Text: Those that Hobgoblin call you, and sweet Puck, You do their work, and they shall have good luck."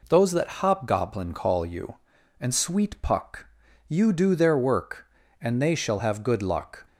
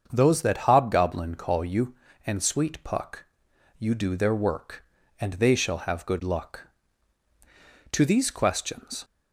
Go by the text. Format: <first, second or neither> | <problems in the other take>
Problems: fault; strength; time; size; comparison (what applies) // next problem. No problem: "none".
first | starts louder than the rest; until 1.1 s; 7 dB // goes on to say "To these questions"; noticeable; from 7.9 s on; 1.1 s long